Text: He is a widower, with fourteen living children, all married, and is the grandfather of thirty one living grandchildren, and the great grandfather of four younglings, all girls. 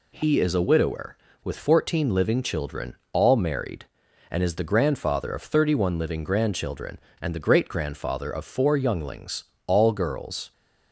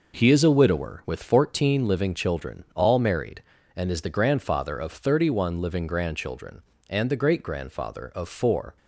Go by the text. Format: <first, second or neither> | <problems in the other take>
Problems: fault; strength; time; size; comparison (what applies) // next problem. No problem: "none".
first | stops before "younglings all girls"; at 8.7 s